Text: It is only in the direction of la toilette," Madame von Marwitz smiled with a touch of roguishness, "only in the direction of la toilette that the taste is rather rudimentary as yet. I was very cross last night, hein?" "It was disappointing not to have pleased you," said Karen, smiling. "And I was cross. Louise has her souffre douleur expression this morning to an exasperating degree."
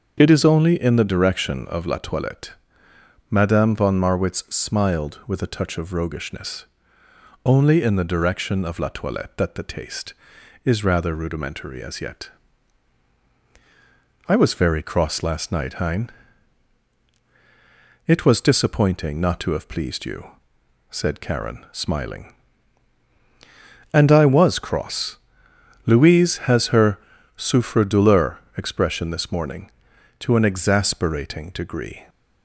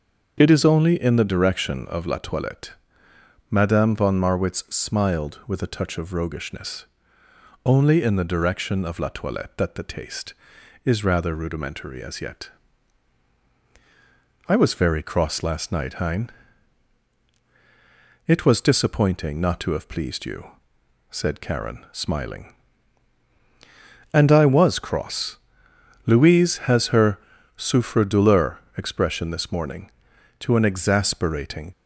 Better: first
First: starts louder than the rest; until 1.2 s; 6.5 dB // pauses between "her" and "souffre"; at 26.9 s; 0.38 s long // pauses between "douleur" and "expression"; slight; at 28.3 s; 0.18 s long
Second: starts louder than the rest; until 1.4 s; 6.5 dB // pauses between "her" and "souffre"; at 27.1 s; 0.38 s long // pauses between "douleur" and "expression"; slight; at 28.5 s; 0.18 s long // stops before "degree"; at 31.7 s

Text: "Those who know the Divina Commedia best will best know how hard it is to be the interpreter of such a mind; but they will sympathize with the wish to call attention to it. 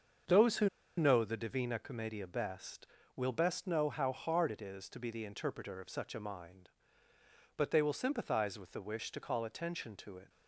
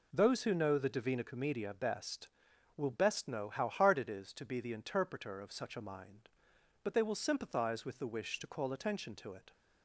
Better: second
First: starts louder than the rest; until 1.5 s; 6.5 dB // pauses between "who" and "know"; slight; at 0.6 s; 0.29 s long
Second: none

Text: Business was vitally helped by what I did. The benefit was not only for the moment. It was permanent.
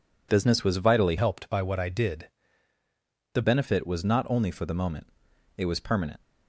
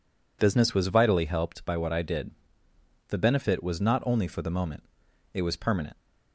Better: second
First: changes voice from "helped" to "The"; from 1.1 to 3.4 s; 2.3 s long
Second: none

